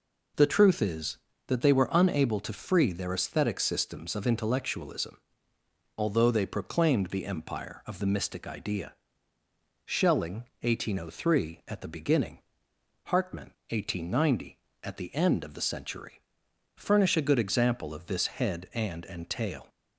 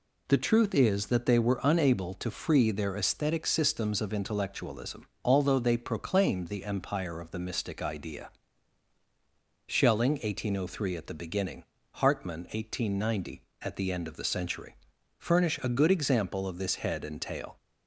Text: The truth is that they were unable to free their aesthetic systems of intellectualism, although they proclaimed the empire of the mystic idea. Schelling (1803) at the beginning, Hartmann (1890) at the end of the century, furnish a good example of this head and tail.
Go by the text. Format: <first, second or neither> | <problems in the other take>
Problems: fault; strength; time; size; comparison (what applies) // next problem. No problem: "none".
second | says "and" twice; at 19.0 s